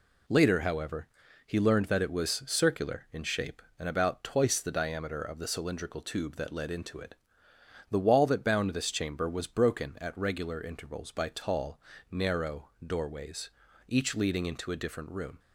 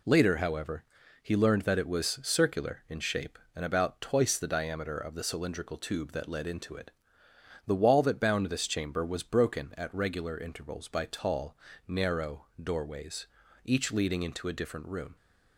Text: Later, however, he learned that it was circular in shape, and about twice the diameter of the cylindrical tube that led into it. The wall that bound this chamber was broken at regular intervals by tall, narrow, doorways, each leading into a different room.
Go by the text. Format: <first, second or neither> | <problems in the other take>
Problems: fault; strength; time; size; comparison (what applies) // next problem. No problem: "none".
neither | none